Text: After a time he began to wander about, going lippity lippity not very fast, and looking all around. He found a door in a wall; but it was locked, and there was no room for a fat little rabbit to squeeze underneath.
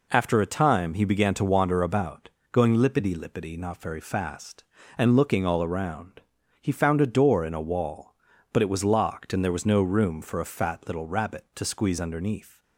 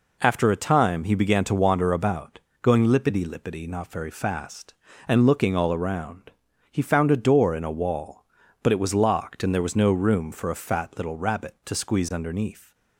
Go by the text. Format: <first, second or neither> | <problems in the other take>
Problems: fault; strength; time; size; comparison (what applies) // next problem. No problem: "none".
neither | none